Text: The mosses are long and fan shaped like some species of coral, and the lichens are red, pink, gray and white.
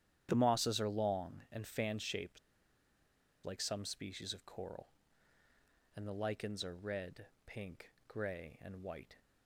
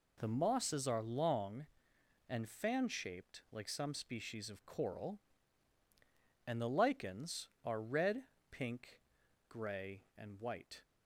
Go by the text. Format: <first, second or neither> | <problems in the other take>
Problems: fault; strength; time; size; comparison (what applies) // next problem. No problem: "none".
second | starts louder than the rest; strong; until 1.3 s; 10.5 dB // pauses between "shaped" and "like"; at 2.3 s; 1.0 s long